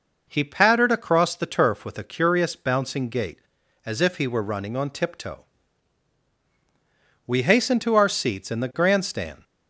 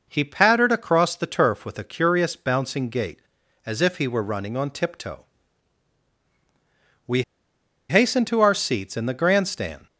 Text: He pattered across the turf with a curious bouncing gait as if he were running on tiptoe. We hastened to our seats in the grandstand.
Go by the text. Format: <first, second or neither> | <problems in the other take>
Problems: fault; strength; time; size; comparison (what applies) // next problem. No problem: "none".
first | pauses between "We" and "hastened"; noticeable; at 7.2 s; 0.66 s long